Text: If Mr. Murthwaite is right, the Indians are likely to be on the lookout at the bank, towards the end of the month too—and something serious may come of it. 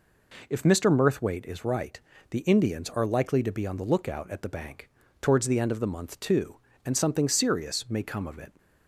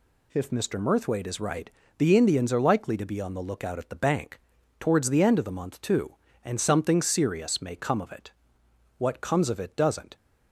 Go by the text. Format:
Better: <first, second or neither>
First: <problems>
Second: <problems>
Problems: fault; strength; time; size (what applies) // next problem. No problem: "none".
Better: first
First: none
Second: goes on to say "What comes of it doesn't"; noticeable; from 8.9 s on; 1.1 s long